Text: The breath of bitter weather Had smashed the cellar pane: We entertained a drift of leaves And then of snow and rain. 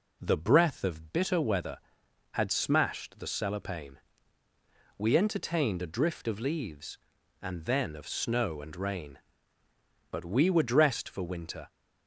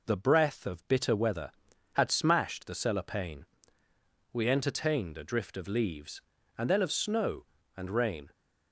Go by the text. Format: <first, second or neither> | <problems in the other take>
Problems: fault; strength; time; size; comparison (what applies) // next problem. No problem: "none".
second | goes on to say "But we were dressed for winter"; from 10.1 s on; 1.5 s long